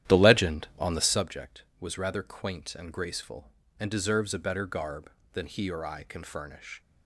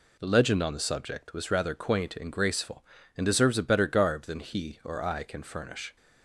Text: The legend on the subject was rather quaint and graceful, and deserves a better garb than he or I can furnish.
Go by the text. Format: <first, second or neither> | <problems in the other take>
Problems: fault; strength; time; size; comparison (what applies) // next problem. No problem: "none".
second | starts louder than the rest; strong; until 1.3 s; 11.5 dB